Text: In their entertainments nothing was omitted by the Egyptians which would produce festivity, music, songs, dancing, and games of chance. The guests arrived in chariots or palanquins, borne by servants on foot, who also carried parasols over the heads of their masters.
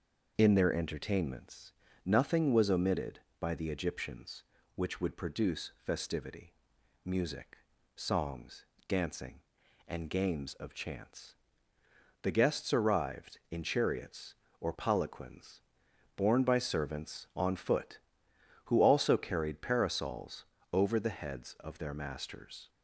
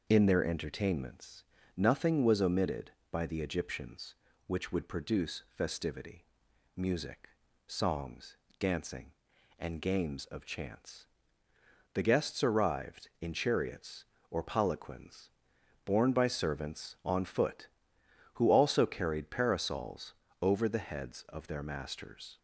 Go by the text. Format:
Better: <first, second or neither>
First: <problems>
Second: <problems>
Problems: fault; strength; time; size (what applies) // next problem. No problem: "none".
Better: neither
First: pauses between "entertainments" and "nothing"; slight; at 1.7 s; 0.32 s long // pauses between "parasols" and "over"; slight; at 20.4 s; 0.26 s long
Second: pauses between "entertainments" and "nothing"; slight; at 1.4 s; 0.32 s long // pauses between "parasols" and "over"; slight; at 20.1 s; 0.26 s long